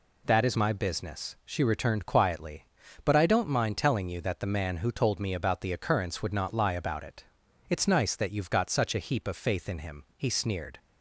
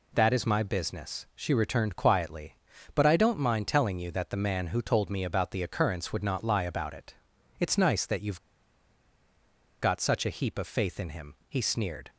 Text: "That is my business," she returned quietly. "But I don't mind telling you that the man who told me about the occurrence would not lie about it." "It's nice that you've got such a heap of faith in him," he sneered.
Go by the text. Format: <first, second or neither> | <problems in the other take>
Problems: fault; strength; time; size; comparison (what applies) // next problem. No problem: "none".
first | pauses between "you've" and "got"; strong; at 8.3 s; 1.4 s long